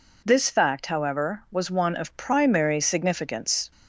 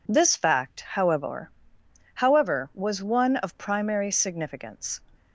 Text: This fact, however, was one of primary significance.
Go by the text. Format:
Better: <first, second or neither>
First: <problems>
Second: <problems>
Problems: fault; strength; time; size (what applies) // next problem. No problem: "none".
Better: first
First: none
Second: says "however" twice; at 2.1 s